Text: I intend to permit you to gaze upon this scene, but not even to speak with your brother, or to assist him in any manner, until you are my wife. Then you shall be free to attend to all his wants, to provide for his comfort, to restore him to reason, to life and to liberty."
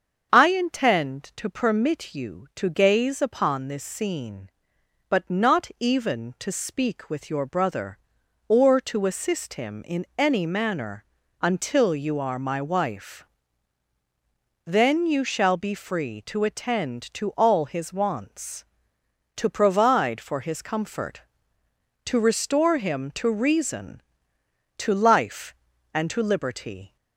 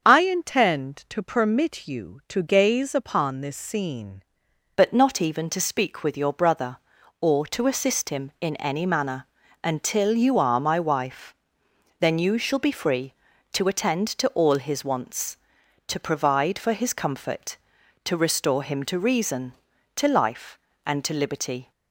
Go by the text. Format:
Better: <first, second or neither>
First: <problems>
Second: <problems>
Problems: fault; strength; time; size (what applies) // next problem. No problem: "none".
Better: first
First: starts louder than the rest; until 1.3 s; 7 dB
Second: starts louder than the rest; until 1.0 s; 7 dB // changes voice at "but"; from 4.7 s on; 17.0 s long